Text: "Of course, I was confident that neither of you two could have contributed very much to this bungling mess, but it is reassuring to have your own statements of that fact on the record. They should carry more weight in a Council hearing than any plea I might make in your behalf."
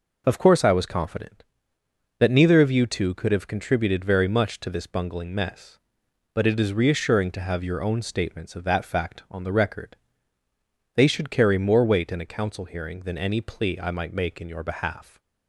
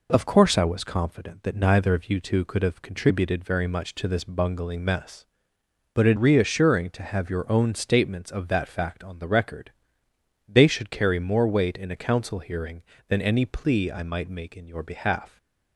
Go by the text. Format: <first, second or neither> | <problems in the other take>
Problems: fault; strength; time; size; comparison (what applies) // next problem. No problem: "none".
first | skips "is"; at 6.1 s